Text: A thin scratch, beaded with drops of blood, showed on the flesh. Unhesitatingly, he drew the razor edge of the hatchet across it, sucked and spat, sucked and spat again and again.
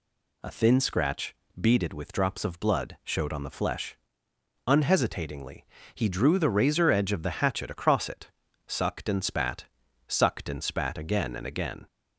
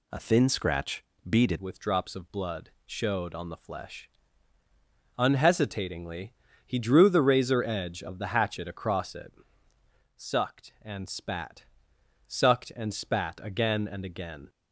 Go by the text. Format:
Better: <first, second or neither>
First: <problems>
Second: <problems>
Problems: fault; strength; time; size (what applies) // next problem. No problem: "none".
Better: first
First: none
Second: changes voice at "with"; from 1.5 s on; 12.9 s long